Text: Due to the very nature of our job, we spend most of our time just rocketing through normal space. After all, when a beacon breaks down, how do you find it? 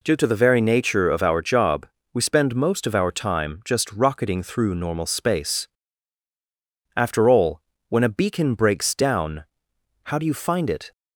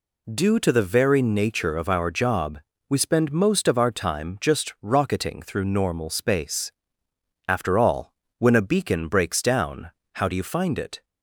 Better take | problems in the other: neither | none

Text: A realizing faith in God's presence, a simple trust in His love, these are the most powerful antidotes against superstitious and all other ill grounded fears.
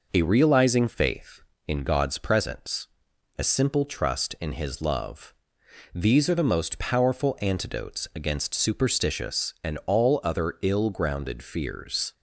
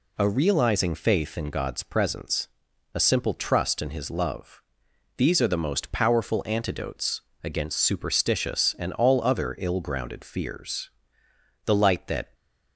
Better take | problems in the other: first | pauses between "antidotes" and "against"; slight; at 7.2 s; 0.20 s long // goes on to say "The light that"; noticeable; from 11.6 s on; 0.68 s long

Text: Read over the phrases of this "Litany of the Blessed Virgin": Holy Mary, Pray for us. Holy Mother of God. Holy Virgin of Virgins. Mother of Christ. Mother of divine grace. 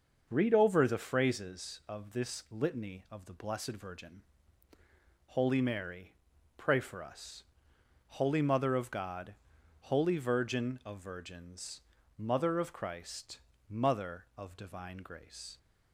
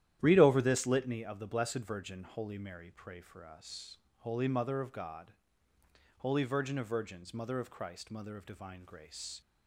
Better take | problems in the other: first | starts louder than the rest; strong; until 1.2 s; 11.5 dB; noticeable in the first // skips "the phrases of"; at 0.6 s

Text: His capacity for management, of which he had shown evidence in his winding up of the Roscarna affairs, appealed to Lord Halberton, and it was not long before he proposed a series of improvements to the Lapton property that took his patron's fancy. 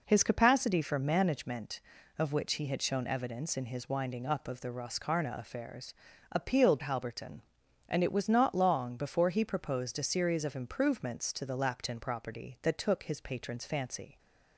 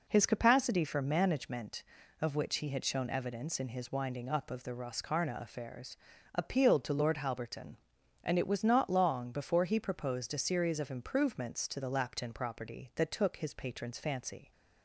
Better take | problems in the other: second | skips "to Lord"; at 6.8 s

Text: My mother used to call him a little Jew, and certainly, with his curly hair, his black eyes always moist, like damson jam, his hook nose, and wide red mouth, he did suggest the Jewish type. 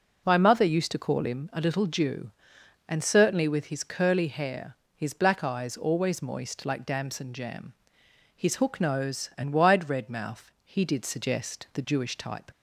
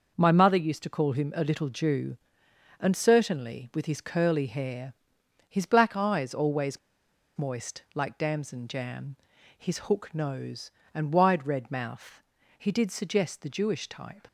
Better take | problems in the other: first | pauses between "always" and "moist"; noticeable; at 6.7 s; 0.60 s long

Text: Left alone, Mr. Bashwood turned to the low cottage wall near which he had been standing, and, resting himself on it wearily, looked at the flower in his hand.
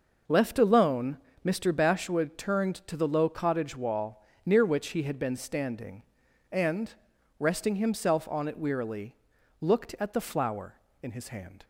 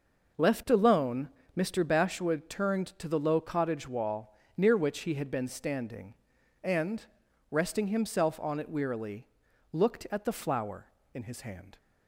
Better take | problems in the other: neither | pauses between "wall" and "near"; slight; the same in both

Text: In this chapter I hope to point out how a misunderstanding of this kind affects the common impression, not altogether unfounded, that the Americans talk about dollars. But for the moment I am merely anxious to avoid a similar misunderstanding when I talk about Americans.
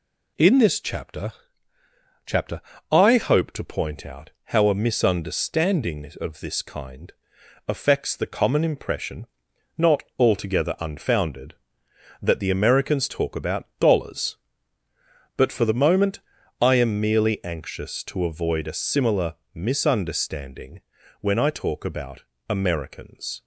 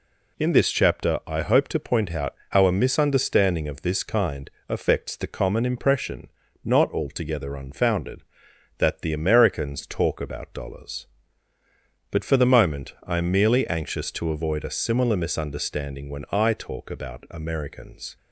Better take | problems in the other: second | says "chapter" twice; at 2.2 s // pauses between "kind" and "affects"; noticeable; at 7.1 s; 0.56 s long; slight in the second // pauses between "not" and "altogether"; slight; at 10.0 s; 0.16 s long // pauses between "moment" and "I"; at 16.1 s; 0.42 s long // pauses between "similar" and "misunderstanding"; slight; at 19.3 s; 0.18 s long // pauses between "misunderstanding" and "when"; at 20.7 s; 0.40 s long // pauses between "about" and "Americans"; slight; at 22.2 s; 0.26 s long

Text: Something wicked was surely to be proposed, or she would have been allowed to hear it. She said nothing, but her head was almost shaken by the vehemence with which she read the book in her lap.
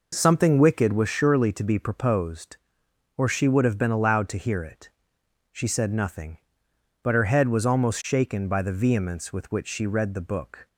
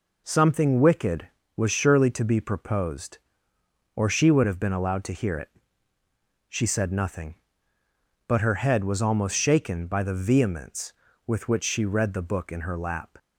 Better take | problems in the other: second | stops before "in her lap"; at 10.6 s

